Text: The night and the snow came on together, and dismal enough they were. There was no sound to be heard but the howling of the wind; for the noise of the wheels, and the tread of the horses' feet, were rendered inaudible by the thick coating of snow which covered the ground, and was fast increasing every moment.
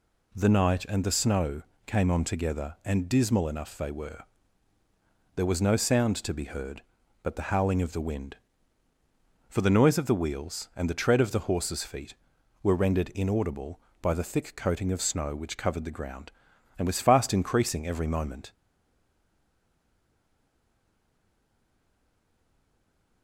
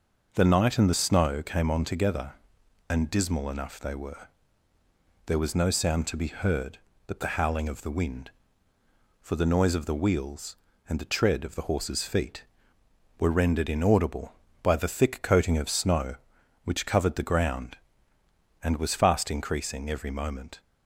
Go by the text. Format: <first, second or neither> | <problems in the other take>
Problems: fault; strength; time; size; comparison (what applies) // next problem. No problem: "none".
second | pauses between "snow" and "came"; slight; at 1.6 s; 0.24 s long // stays silent after the last word; strong; from 18.5 s on; 4.7 s long